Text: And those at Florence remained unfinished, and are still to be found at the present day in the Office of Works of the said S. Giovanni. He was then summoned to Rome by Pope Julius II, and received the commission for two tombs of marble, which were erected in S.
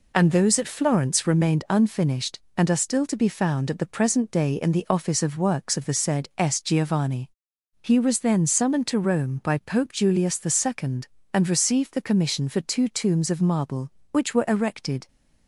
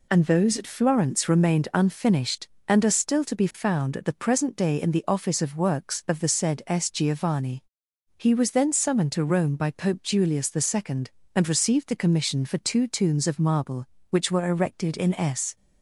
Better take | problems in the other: second | stops before "in S"; at 15.0 s

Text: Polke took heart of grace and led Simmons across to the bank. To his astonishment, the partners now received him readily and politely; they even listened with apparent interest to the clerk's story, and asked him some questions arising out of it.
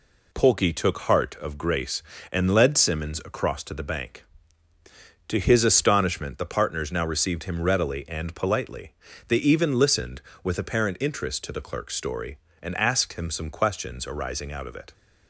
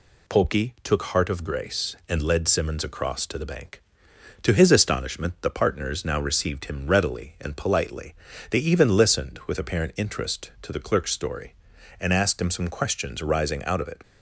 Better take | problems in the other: neither | none

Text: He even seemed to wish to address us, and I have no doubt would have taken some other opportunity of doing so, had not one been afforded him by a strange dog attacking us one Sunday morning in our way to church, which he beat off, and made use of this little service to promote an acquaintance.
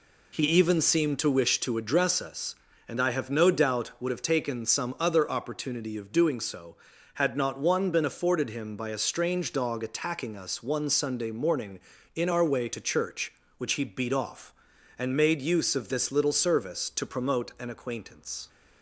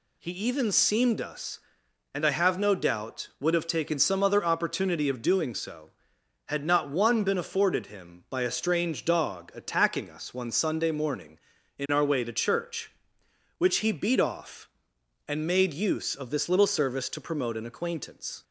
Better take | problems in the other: first | skips "to wish to address"; at 1.2 s

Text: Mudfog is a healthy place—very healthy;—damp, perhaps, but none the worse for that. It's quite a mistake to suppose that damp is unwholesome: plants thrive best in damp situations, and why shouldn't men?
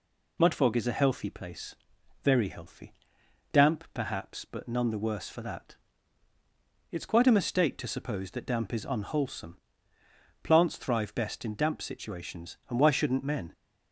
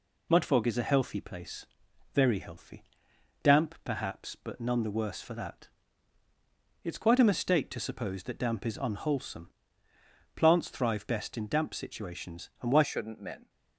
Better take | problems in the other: first | changes voice at "shouldn't"; from 12.8 s on; 0.6 s long

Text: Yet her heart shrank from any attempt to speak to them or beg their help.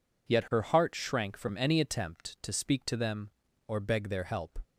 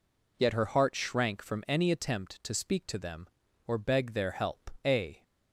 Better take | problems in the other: first | goes on to say "A"; slight; from 4.8 s on; 0.40 s long

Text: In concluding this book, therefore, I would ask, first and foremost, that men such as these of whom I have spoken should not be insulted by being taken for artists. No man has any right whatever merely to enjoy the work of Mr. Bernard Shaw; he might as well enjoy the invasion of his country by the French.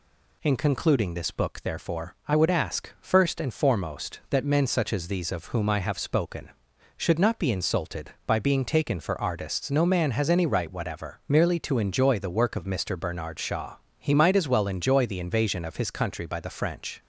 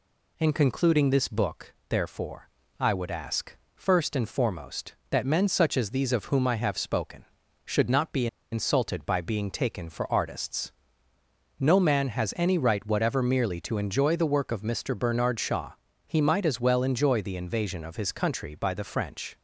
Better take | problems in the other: first | pauses between "be" and "insulted"; slight; at 8.2 s; 0.25 s long

